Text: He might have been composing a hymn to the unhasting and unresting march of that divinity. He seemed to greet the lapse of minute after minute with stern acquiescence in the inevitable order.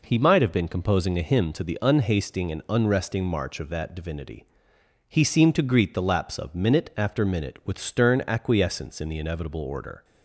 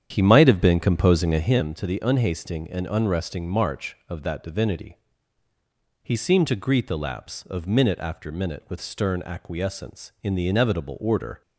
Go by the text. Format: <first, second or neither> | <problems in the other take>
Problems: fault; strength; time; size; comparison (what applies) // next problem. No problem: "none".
first | starts louder than the rest; strong; until 1.6 s; 9 dB